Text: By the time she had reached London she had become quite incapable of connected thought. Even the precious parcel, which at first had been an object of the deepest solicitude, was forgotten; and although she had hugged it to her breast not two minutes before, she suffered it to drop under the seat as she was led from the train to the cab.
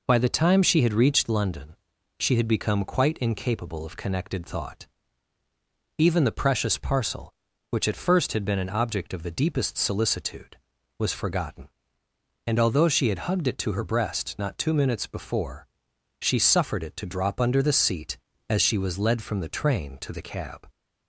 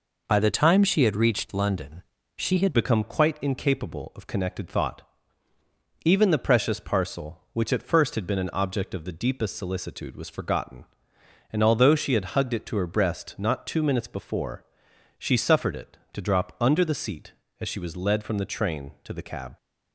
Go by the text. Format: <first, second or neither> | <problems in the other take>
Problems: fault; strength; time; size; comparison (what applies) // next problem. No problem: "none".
first | pauses between "London" and "she"; slight; at 2.0 s; 0.32 s long; also in the first // changes voice at "become"; from 2.7 s on; 16.8 s long